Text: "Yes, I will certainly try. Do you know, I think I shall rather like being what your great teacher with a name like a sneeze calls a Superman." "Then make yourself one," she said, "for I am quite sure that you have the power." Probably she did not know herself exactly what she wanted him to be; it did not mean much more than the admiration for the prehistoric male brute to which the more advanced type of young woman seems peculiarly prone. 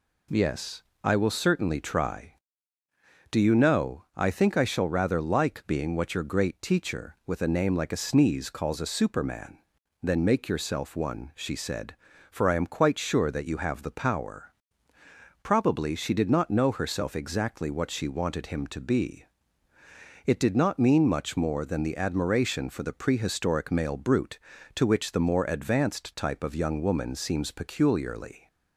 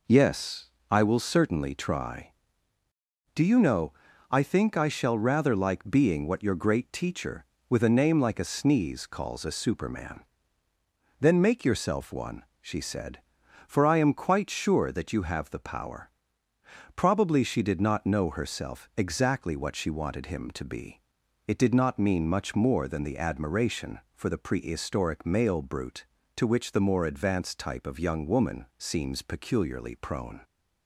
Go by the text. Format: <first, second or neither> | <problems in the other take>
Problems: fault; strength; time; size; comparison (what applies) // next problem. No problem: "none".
second | stops before "prone"; at 28.4 s